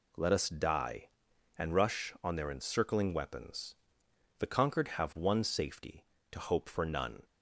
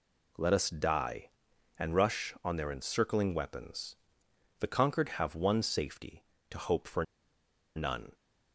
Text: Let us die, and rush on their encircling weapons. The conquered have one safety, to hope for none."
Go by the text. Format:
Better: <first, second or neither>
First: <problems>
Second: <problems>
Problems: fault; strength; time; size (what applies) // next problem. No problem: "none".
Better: first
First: none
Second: pauses between "for" and "none"; noticeable; at 7.0 s; 0.72 s long